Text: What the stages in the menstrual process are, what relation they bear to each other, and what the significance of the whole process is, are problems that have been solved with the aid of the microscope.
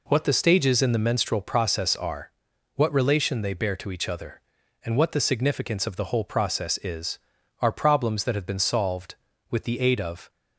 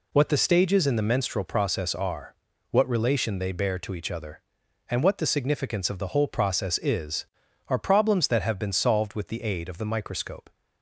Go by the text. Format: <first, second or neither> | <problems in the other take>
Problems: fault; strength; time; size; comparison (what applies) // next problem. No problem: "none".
second | stops before "the microscope"; at 10.3 s